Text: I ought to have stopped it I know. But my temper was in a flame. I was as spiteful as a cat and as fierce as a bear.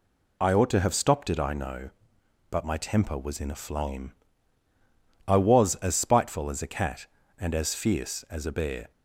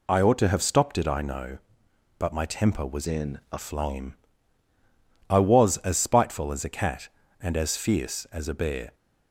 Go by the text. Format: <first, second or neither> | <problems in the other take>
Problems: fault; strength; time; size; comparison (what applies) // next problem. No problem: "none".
first | changes voice from "in" to "a"; from 3.0 to 3.5 s; 0.5 s long